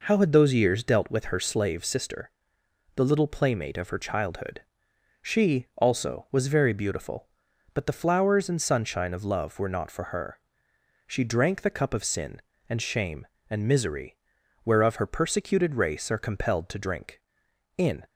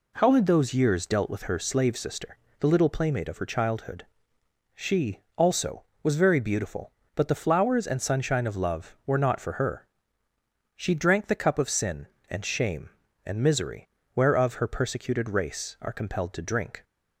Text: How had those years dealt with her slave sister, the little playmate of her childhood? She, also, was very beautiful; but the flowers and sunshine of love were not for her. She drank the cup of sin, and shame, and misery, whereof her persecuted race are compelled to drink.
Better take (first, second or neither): second